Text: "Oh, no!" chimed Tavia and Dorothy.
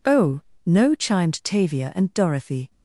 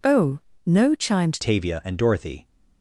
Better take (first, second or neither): first